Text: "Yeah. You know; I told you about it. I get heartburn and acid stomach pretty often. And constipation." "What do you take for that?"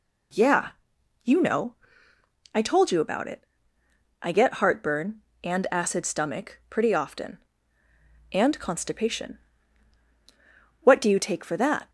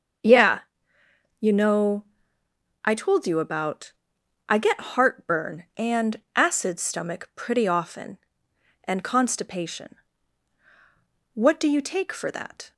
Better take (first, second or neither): first